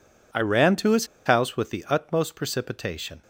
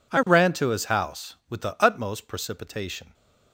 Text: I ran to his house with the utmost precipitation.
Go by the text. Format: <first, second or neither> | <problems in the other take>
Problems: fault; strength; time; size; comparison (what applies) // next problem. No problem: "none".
second | pauses between "his" and "house"; slight; at 1.0 s; 0.20 s long